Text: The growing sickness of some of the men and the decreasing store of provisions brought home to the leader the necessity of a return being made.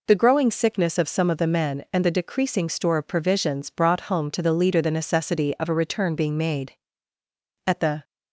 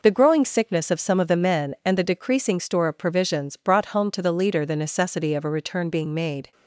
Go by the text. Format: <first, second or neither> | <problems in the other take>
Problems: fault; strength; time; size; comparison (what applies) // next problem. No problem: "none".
second | goes on to say "At the"; slight; from 7.6 s on; 0.36 s long